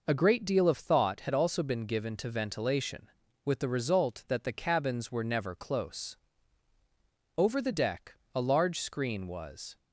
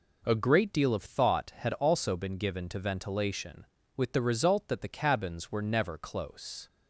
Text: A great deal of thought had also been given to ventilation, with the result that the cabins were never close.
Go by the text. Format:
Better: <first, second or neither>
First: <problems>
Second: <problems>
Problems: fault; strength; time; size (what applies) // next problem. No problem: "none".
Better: second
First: goes on to say "Over the deck a large screen was"; strong; from 7.3 s on; 2.3 s long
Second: none